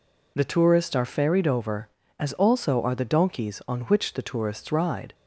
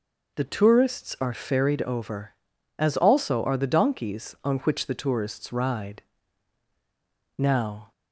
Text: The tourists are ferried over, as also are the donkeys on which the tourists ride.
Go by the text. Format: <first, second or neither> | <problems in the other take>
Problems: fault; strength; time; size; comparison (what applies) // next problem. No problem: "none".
first | goes on to say "Now"; from 7.3 s on; 0.54 s long